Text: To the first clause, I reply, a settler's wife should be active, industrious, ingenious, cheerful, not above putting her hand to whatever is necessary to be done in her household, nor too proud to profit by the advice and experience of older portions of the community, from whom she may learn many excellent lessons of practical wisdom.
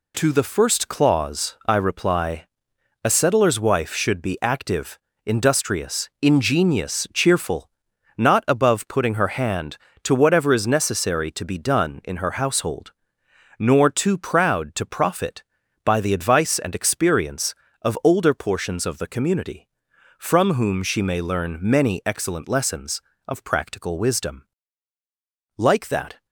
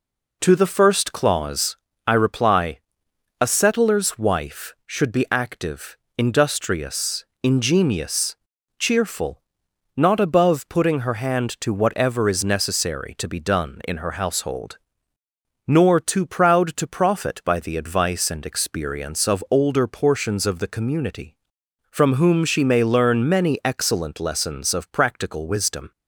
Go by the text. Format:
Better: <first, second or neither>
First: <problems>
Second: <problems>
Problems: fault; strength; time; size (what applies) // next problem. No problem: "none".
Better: second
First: goes on to say "Like that"; noticeable; from 25.5 s on; 0.68 s long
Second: none